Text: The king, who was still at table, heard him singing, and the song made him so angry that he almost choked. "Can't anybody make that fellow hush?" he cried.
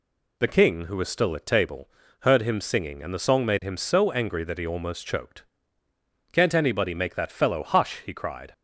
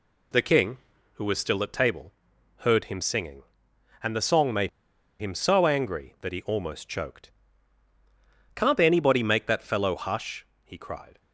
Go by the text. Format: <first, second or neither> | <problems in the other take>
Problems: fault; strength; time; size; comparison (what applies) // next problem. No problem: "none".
first | pauses between "made" and "him"; noticeable; at 4.6 s; 0.50 s long